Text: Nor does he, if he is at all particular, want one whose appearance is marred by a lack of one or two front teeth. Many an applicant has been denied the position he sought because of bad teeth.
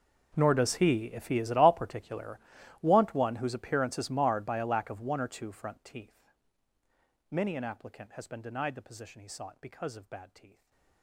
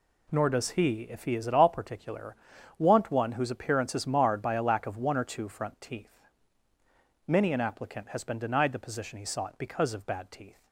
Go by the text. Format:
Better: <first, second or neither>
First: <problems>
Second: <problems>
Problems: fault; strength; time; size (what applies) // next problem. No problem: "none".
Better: second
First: gets quieter; strong; throughout; 23 dB // stays silent after the last word; slight; from 10.4 s on; 0.6 s long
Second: none